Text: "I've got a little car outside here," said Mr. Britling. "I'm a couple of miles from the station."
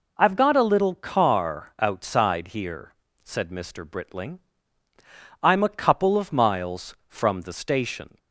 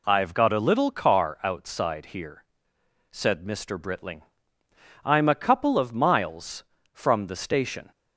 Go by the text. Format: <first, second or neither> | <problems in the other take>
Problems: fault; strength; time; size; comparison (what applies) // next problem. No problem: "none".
neither | none